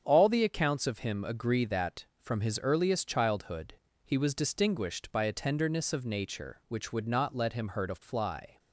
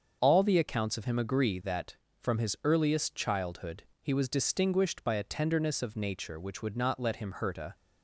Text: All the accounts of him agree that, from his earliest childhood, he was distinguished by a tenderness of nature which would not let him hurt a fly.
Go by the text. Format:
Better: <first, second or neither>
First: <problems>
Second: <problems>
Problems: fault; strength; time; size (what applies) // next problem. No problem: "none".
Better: first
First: starts louder than the rest; strong; until 1.0 s; 7.5 dB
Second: starts louder than the rest; until 1.2 s; 6.5 dB // stops before "fly"; at 7.7 s